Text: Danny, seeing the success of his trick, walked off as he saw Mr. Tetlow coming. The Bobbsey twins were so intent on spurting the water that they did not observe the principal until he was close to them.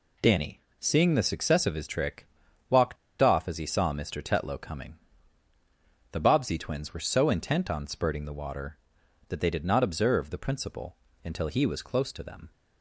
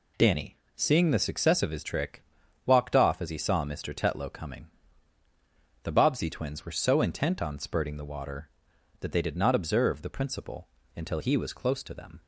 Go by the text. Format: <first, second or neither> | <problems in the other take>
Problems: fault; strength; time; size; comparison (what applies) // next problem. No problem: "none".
second | pauses between "walked" and "off"; slight; at 2.9 s; 0.24 s long // pauses between "principal" and "until"; slight; at 10.9 s; 0.26 s long; slight in the second